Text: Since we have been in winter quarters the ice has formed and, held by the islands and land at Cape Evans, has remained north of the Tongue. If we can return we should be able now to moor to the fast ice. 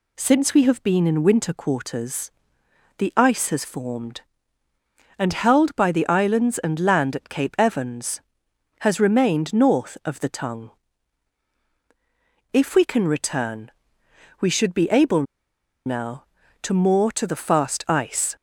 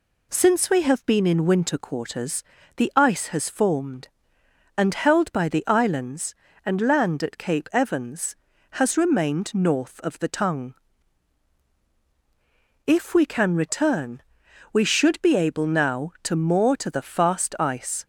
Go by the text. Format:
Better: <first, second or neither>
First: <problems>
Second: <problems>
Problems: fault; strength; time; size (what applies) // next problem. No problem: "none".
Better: second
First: pauses between "quarters" and "the"; noticeable; at 2.3 s; 0.66 s long // pauses between "return" and "we"; noticeable; at 13.7 s; 0.68 s long // pauses between "able" and "now"; noticeable; at 15.2 s; 0.62 s long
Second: pauses between "quarters" and "the"; slight; at 2.4 s; 0.32 s long // pauses between "return" and "we"; noticeable; at 14.1 s; 0.54 s long